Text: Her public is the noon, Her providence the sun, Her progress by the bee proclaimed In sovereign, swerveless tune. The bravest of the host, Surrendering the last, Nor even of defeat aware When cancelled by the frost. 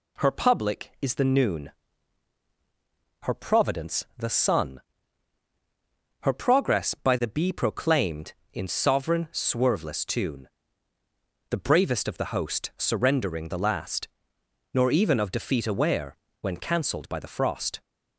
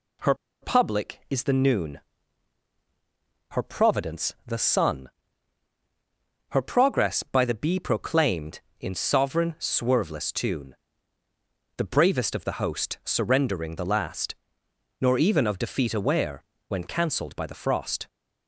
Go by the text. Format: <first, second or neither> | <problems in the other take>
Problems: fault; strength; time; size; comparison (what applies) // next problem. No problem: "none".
first | pauses between "Her" and "public"; slight; at 0.3 s; 0.27 s long // pauses between "aware" and "When"; slight; at 16.4 s; 0.24 s long; slight in the first